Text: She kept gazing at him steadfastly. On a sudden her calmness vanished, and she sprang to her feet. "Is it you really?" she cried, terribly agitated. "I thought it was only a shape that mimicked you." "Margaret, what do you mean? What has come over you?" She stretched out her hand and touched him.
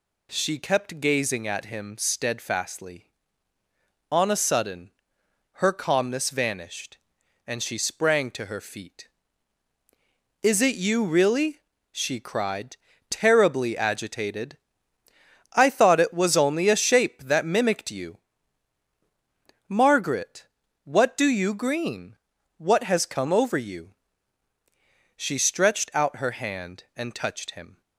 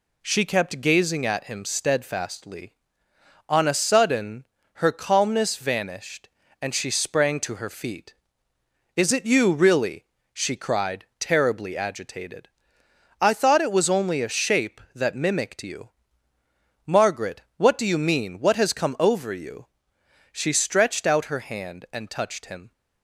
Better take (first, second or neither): second